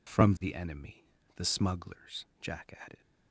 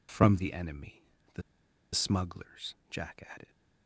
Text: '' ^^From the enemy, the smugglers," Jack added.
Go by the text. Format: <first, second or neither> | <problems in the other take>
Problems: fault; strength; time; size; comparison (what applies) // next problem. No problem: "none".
first | pauses between "the" and "smugglers"; noticeable; at 1.4 s; 0.52 s long